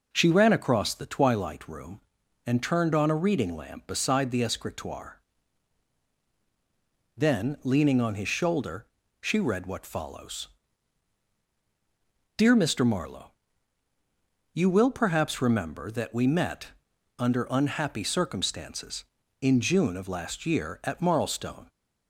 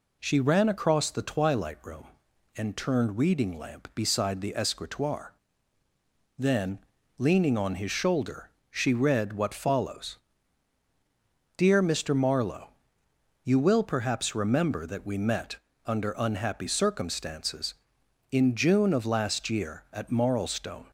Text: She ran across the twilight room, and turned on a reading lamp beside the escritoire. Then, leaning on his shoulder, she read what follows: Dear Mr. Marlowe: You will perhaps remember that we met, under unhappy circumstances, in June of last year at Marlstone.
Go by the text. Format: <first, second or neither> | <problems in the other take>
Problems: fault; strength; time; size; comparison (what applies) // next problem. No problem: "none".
first | skips "on a"; at 3.1 s